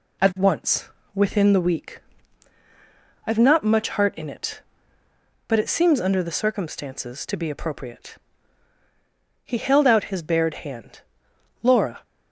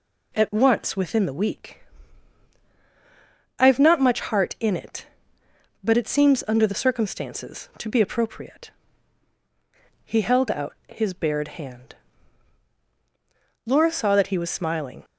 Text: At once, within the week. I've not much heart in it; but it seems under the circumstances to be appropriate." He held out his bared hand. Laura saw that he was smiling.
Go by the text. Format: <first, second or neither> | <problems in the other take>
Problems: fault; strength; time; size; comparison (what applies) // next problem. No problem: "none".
second | stops before "saw that he was smiling"; at 12.0 s